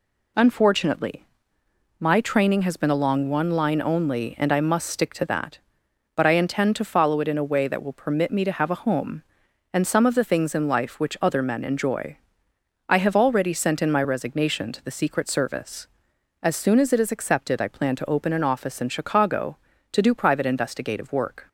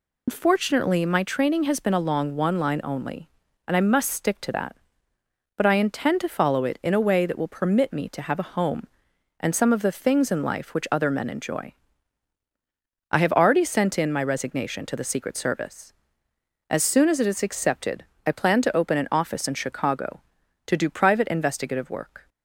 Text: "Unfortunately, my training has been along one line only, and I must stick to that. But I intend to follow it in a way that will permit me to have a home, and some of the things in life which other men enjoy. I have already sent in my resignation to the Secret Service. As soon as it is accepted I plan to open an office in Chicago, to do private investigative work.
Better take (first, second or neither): first